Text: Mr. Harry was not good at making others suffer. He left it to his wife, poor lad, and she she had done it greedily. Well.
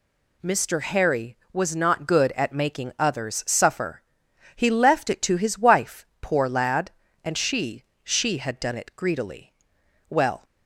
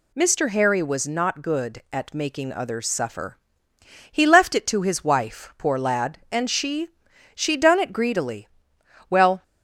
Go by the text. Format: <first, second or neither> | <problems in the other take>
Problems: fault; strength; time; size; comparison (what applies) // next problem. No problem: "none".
first | pauses between "she" and "she"; noticeable; at 6.8 s; 0.46 s long; slight in the first // skips "had"; at 7.5 s